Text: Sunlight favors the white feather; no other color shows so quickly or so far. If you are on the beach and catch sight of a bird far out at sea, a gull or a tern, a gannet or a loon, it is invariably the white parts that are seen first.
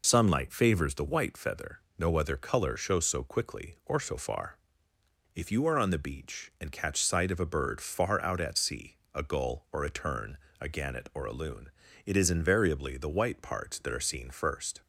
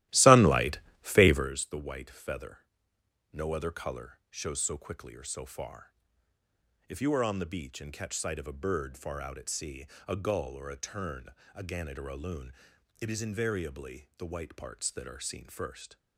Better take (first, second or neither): first